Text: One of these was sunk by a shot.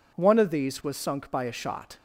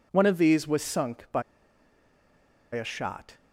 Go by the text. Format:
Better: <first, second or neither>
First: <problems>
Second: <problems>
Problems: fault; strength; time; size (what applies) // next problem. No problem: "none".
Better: first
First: none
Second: pauses between "by" and "a"; strong; at 1.4 s; 1.3 s long